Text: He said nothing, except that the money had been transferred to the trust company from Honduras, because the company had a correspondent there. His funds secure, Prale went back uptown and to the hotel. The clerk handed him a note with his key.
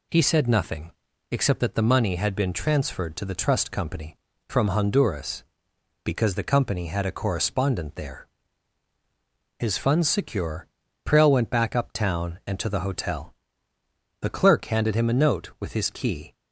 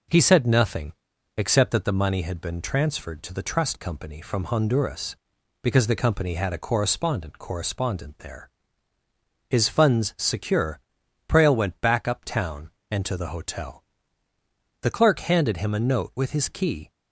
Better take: first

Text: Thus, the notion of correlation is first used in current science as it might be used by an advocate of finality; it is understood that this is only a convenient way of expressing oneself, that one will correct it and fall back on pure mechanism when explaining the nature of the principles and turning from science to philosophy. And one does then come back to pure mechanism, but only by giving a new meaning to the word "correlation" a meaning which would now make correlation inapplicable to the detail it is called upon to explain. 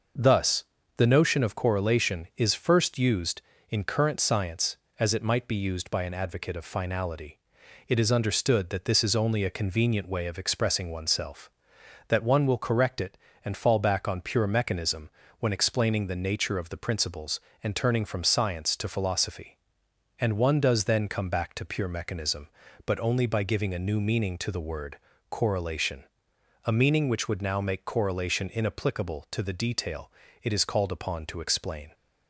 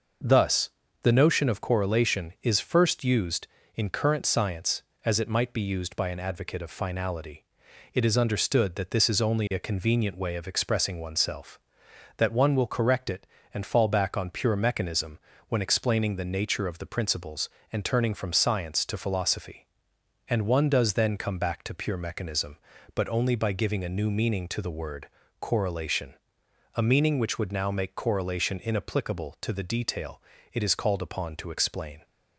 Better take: neither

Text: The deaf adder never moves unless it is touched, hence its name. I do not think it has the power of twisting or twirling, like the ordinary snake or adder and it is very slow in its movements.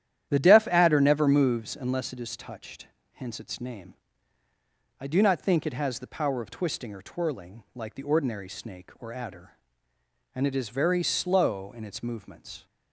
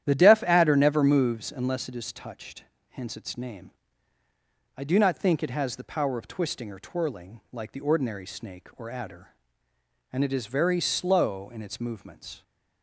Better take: neither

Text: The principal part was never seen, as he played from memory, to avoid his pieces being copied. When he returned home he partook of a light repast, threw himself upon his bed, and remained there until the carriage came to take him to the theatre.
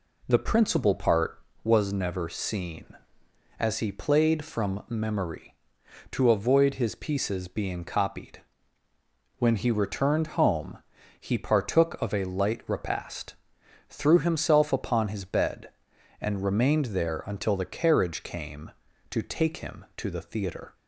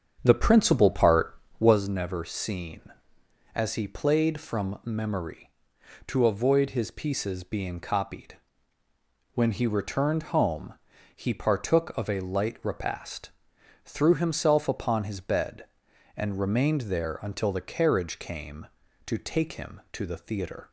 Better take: first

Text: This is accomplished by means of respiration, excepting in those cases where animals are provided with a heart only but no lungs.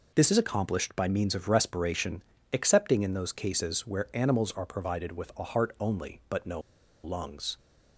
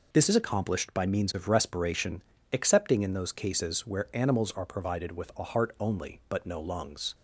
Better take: second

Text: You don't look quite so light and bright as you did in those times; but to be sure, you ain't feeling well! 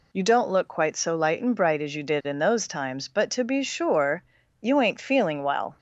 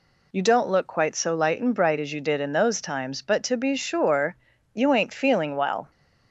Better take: neither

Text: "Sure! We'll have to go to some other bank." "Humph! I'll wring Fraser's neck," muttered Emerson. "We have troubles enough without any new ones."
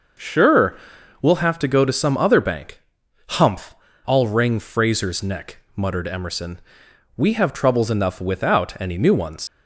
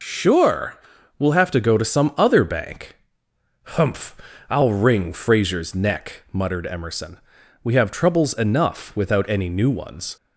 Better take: second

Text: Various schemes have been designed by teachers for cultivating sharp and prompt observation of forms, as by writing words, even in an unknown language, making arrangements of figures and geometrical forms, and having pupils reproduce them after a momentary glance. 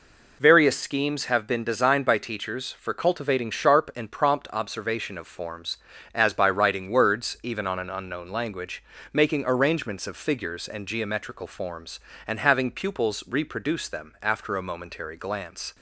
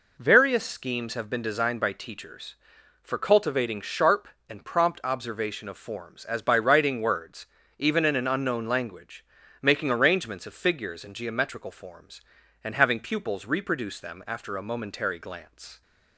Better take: second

